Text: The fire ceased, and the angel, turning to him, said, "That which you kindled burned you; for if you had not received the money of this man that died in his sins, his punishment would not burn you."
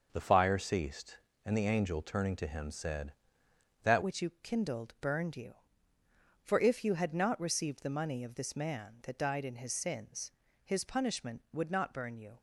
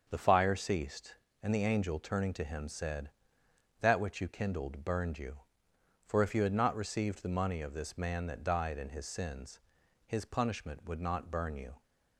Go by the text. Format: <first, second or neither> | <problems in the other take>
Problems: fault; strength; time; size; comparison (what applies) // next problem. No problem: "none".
second | starts louder than the rest; noticeable; until 1.1 s; 6 dB; also in the second // changes voice at "which"; from 4.0 s on; 8.3 s long